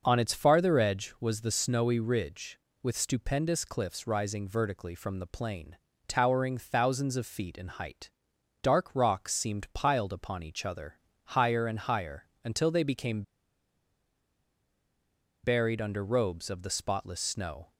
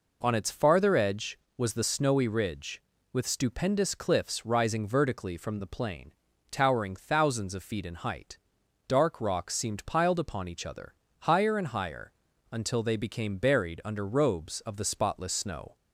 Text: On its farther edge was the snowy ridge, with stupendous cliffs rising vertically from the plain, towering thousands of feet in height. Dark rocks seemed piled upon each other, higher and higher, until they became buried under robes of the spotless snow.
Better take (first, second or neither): second